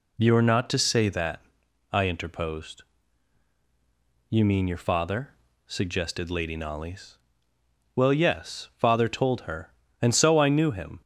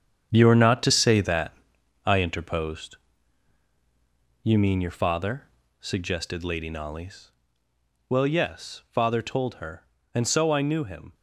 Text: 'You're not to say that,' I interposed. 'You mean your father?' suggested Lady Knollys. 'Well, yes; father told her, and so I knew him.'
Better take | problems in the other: first | gets quieter; strong; throughout; 9 dB

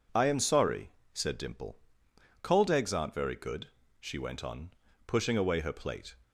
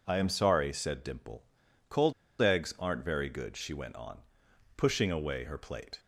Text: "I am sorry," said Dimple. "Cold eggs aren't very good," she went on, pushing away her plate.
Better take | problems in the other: first | pauses between "Cold" and "eggs"; slight; at 2.1 s; 0.28 s long

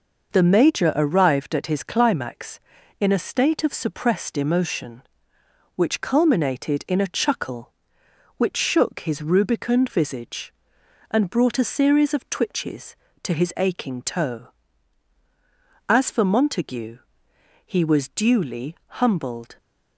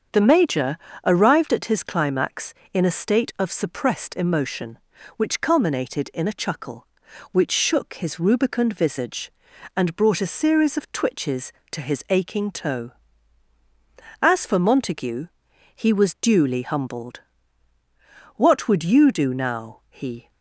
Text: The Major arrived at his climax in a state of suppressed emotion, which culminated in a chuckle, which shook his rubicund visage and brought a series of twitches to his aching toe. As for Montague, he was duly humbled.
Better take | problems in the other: first | starts louder than the rest; strong; until 1.4 s; 7 dB // pauses between "Major" and "arrived"; slight; at 0.7 s; 0.30 s long // goes on to say "What would you do now he"; strong; from 18.3 s on; 1.9 s long

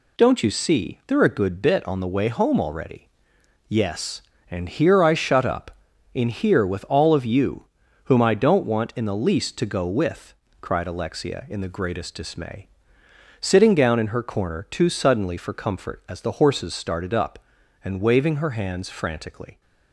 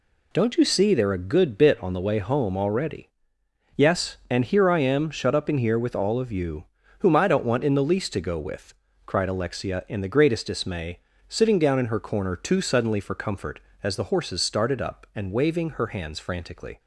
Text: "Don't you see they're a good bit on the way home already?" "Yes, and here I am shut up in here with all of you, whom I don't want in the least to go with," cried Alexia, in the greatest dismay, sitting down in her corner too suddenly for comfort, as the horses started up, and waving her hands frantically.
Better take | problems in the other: second | skips "am"; at 5.1 s

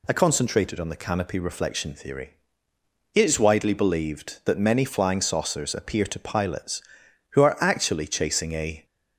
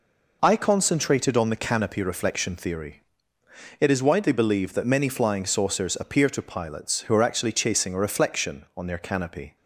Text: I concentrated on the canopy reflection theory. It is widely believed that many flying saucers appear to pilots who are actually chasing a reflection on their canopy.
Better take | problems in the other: second | stops before "reflection on their canopy"; at 8.8 s

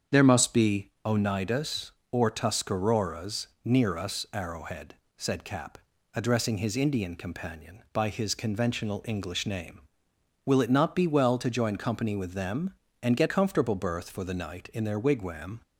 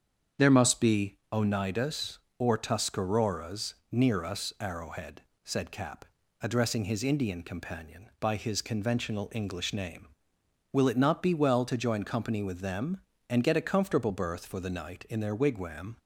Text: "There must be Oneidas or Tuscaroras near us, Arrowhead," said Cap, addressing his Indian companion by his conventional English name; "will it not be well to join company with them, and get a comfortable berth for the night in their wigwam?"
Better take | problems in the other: second | starts louder than the rest; strong; until 1.2 s; 7.5 dB; strong in the second // pauses between "Tuscaroras" and "near"; slight; at 3.4 s; 0.18 s long; slight in the second // skips "a"; at 13.2 s

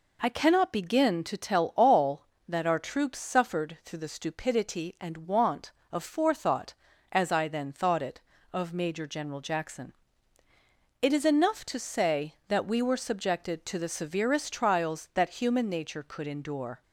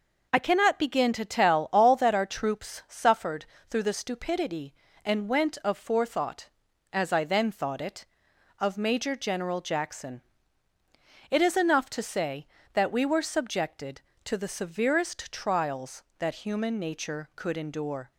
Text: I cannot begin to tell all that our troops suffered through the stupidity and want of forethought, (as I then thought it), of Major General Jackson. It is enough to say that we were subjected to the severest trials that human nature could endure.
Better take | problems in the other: first | pauses between "suffered" and "through"; slight; at 3.4 s; 0.24 s long // says "went" for "want"; at 5.2 s

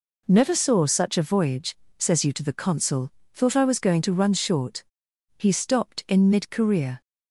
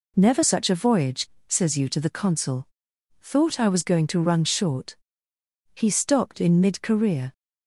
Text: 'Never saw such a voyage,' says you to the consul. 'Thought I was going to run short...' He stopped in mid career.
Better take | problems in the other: first | skips "saw"; at 0.4 s

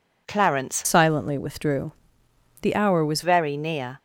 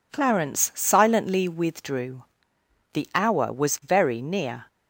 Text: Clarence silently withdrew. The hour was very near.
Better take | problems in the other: second | changes voice from "silently" to "was"; from 0.8 to 3.2 s; 2.4 s long

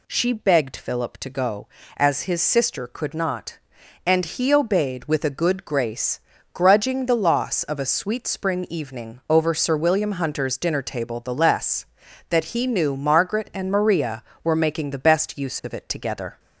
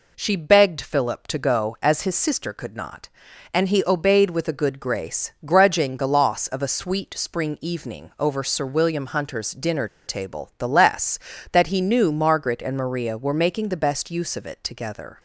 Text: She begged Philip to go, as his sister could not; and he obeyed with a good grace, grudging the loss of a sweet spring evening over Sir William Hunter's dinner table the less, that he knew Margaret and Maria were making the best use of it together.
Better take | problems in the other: first | pauses between "dinner" and "table"; slight; at 9.8 s; 0.19 s long

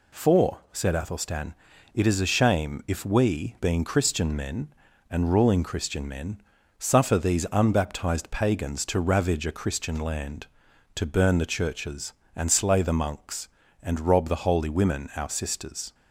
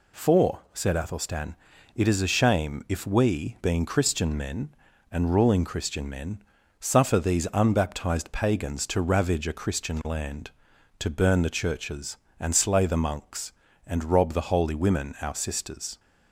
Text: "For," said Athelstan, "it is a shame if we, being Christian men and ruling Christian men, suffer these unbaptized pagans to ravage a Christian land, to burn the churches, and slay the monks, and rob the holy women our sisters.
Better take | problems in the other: neither | none

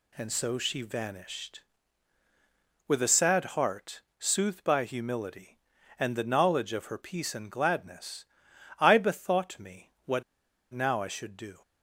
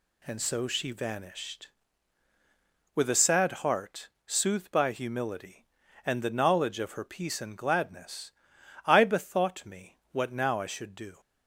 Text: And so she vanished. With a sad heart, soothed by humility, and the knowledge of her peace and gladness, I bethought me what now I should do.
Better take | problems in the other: second | pauses between "me" and "what"; slight; at 9.8 s; 0.16 s long; slight in the second // pauses between "what" and "now"; noticeable; at 10.2 s; 0.50 s long

